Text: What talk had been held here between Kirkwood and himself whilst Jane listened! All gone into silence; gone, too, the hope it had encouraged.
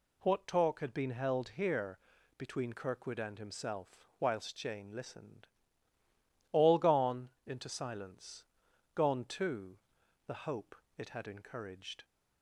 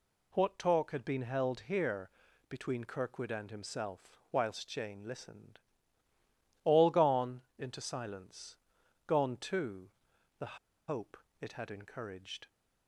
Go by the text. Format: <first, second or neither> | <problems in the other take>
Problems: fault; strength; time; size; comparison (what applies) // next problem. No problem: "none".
first | pauses between "here" and "between"; at 2.0 s; 0.40 s long; also in the first // pauses between "gone" and "into"; slight; at 7.4 s; 0.16 s long; slight in the first // pauses between "the" and "hope"; slight; at 10.5 s; 0.30 s long // pauses between "hope" and "it"; slight; at 11.1 s; 0.24 s long; slight in the first